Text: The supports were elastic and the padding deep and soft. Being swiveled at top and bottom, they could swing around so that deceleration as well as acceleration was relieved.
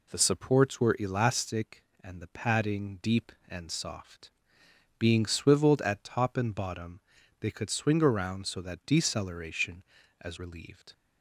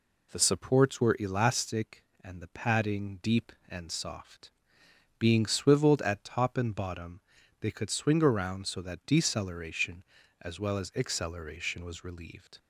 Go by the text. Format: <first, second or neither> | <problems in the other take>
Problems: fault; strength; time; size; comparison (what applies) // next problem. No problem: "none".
second | skips "well as acceleration was"; at 10.3 s